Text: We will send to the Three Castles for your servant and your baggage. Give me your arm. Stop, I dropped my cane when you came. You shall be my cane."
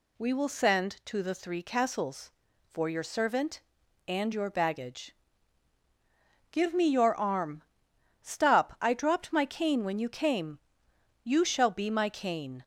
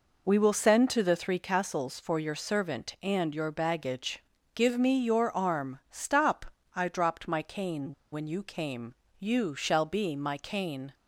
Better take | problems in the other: first | pauses between "cane" and "when"; slight; at 7.9 s; 0.18 s long

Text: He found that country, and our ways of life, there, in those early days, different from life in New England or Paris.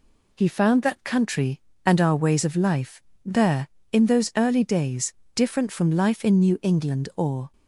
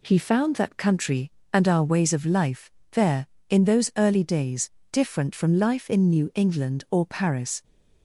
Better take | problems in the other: second | stops before "Paris"; at 7.5 s

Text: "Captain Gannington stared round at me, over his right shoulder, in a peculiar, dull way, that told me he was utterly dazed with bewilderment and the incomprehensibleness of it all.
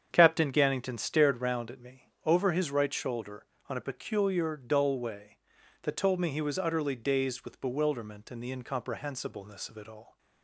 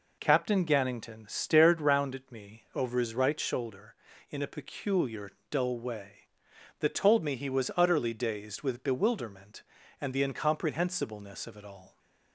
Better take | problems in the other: second | starts louder than the rest; strong; until 1.1 s; 8 dB // says "on" for "in"; at 3.6 s

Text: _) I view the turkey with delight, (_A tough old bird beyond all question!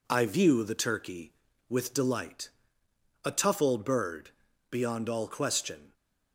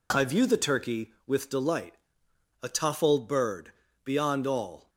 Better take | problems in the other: first | pauses between "bird" and "beyond"; slight; at 3.7 s; 0.32 s long; also in the first // stops before "question"; at 4.8 s

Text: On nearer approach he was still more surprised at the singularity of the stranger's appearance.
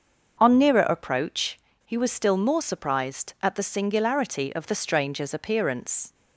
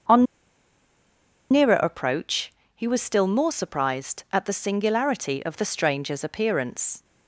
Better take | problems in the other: first | starts louder than the rest; until 2.3 s; 6.5 dB; also in the first // pauses between "On" and "nearer"; strong; at 0.2 s; 1.2 s long // pauses between "approach" and "he"; slight; at 2.5 s; 0.24 s long; slight in the first

